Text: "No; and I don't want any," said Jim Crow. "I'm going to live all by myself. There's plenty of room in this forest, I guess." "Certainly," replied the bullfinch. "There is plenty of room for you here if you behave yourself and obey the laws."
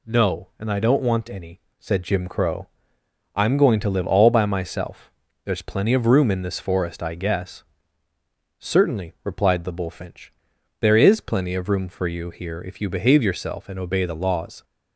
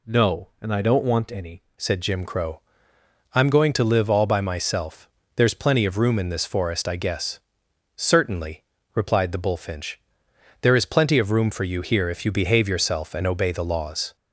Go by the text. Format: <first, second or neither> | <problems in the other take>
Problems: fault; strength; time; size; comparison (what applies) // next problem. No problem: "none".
first | changes voice at "said"; from 1.7 s on; 12.4 s long